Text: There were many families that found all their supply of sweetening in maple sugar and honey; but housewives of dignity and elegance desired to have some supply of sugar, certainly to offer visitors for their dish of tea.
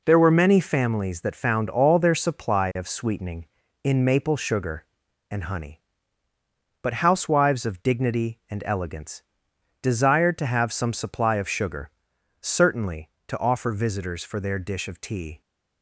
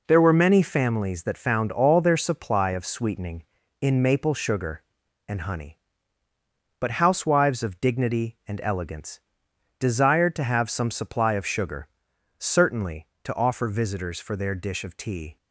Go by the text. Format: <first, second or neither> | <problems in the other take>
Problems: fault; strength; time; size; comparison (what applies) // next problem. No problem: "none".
neither | pauses between "elegance" and "desired"; noticeable; the same in both